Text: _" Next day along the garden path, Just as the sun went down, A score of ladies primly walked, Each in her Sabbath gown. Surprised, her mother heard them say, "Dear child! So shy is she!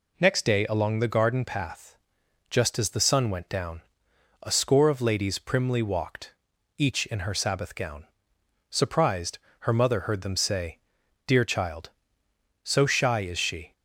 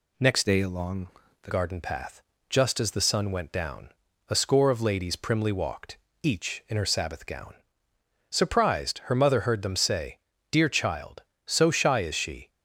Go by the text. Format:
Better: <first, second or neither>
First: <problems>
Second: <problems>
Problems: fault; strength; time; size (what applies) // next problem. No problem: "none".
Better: first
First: none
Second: changes voice from "day" to "the"; from 0.4 to 1.5 s; 1.1 s long // pauses between "along" and "the"; slight; at 1.0 s; 0.32 s long